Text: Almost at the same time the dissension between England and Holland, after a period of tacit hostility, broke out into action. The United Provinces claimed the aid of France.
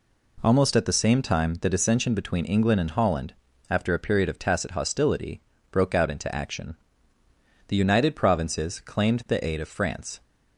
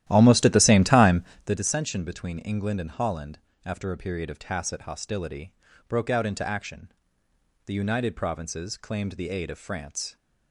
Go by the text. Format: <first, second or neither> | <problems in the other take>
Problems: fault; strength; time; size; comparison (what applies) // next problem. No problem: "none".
first | starts louder than the rest; strong; until 1.6 s; 13 dB // pauses between "time" and "the"; slight; at 1.2 s; 0.24 s long